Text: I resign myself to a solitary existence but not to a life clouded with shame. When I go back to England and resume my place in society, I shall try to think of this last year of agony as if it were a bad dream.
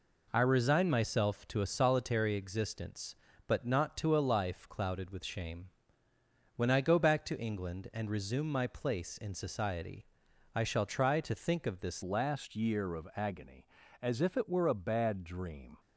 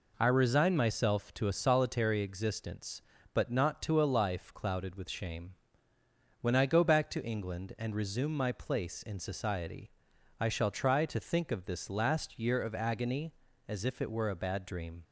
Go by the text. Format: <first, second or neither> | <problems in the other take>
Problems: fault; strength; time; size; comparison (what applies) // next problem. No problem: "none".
second | changes voice at "last"; from 12.0 s on; 3.7 s long